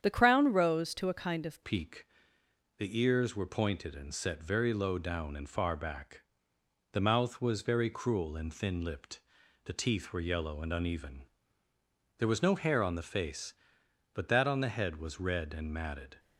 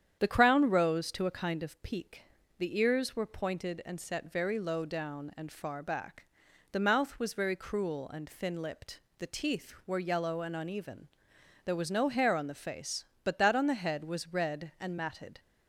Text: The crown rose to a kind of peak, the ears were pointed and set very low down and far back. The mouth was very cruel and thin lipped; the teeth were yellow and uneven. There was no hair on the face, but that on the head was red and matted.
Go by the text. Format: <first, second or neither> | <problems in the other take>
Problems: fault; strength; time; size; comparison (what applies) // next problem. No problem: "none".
second | starts louder than the rest; strong; until 1.0 s; 9 dB; strong in the second // changes voice at "peak"; from 1.6 s on; 14.5 s long